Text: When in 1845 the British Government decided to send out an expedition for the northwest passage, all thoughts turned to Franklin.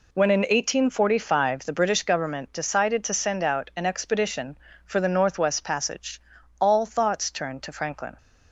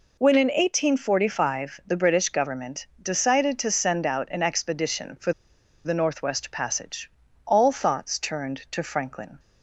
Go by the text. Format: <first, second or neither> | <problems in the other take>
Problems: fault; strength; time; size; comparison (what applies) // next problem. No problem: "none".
first | pauses between "for" and "the"; noticeable; at 5.3 s; 0.53 s long